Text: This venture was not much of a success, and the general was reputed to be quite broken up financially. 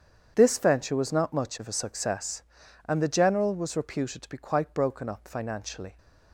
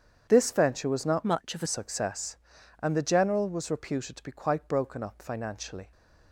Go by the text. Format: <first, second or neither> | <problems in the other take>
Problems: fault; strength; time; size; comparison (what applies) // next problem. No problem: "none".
first | starts louder than the rest; strong; until 1.3 s; 8 dB; strong in the first // changes voice from "much" to "a"; from 1.2 to 1.6 s; 0.4 s long